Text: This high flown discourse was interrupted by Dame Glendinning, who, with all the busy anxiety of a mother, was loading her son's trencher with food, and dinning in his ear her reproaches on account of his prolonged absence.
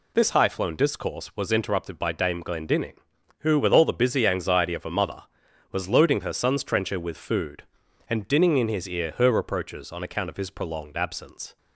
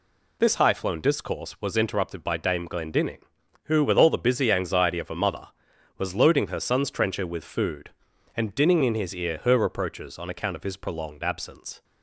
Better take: neither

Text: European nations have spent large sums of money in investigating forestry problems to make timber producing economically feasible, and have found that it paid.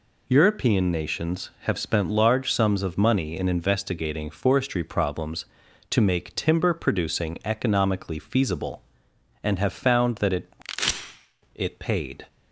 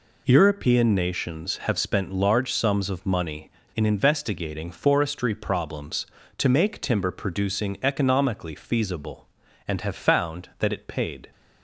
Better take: second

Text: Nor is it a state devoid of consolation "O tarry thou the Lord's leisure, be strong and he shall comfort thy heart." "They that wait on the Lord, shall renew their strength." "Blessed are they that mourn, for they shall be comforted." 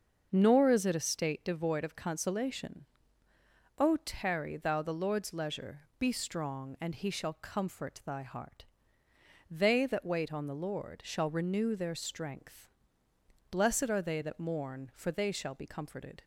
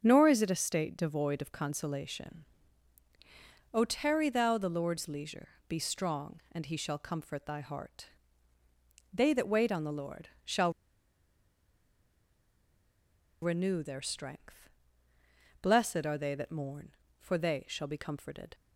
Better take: first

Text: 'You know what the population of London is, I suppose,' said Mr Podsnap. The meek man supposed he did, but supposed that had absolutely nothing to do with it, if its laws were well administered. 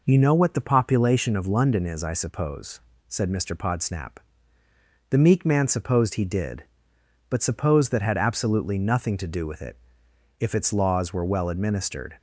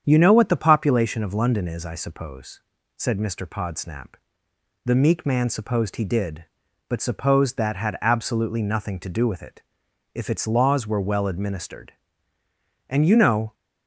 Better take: first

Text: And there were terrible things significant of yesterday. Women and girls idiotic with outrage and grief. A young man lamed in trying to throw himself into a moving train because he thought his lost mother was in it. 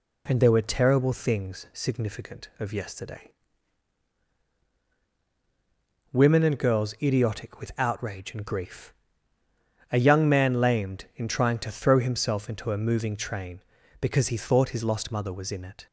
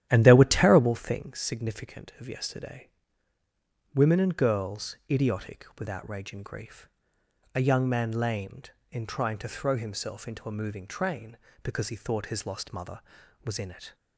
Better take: first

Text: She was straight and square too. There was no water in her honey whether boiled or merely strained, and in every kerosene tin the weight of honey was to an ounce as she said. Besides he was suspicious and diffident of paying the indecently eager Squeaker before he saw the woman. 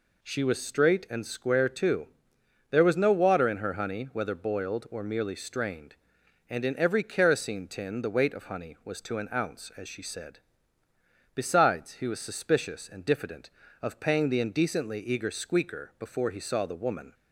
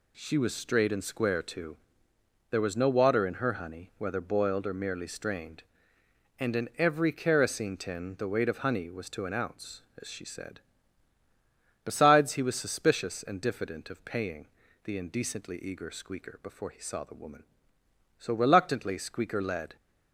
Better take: first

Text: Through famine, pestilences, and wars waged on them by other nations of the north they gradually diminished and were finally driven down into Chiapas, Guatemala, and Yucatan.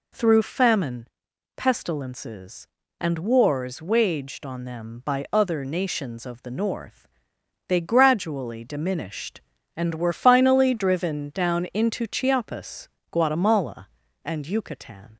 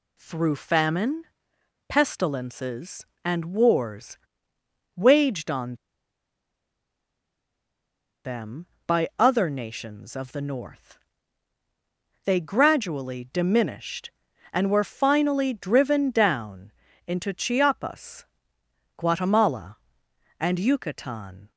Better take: first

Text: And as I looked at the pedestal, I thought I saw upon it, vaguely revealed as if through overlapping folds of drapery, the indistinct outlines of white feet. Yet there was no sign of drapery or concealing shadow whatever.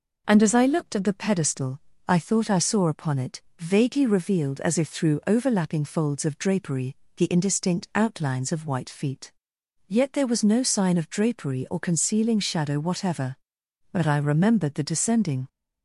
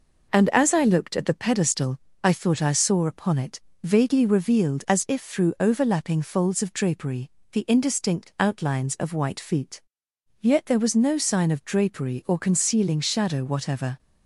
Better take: second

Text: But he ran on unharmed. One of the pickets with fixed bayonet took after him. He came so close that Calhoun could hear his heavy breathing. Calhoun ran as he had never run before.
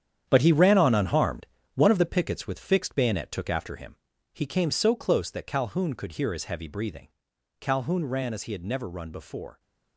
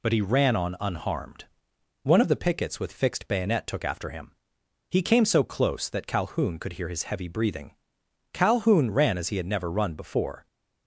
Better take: second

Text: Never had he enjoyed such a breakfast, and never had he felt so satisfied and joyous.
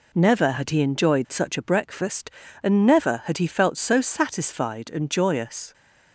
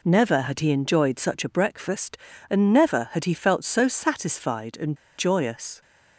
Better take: first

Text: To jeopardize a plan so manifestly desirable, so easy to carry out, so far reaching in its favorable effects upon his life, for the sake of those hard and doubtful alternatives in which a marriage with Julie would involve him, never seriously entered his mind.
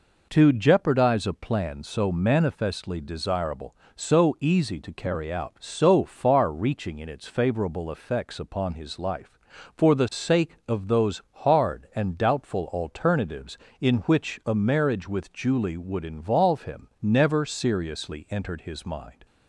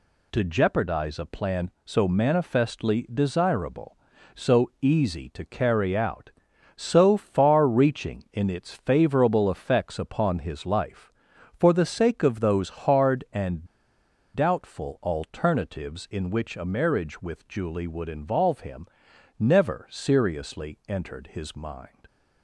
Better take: first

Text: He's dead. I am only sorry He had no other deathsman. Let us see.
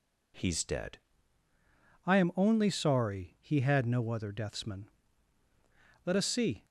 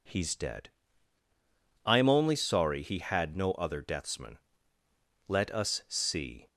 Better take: second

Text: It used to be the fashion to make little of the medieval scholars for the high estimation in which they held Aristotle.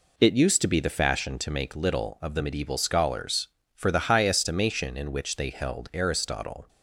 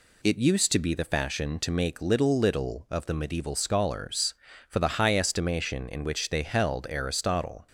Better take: first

